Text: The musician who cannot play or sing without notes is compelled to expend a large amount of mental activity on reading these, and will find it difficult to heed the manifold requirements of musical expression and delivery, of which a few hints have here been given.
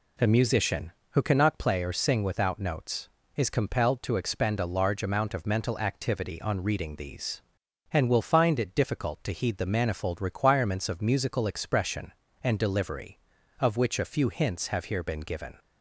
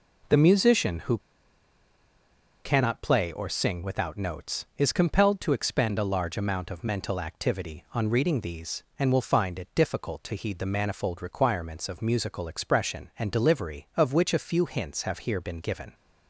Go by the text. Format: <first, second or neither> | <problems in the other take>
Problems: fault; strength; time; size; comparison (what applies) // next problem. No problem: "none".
first | pauses between "who" and "cannot"; strong; at 1.1 s; 1.4 s long